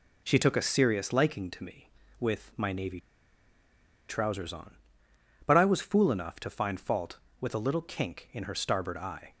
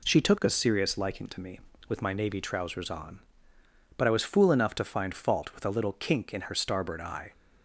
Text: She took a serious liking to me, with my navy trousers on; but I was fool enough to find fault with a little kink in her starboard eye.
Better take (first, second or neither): second